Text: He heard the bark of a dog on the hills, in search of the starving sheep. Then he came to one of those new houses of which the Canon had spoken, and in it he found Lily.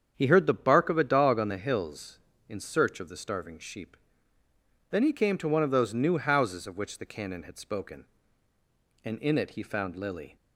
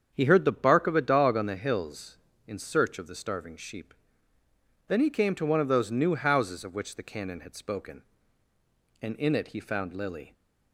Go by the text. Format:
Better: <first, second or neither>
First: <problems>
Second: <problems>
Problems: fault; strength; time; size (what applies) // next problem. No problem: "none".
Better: neither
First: starts louder than the rest; strong; until 1.1 s; 8 dB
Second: starts louder than the rest; strong; until 1.1 s; 8 dB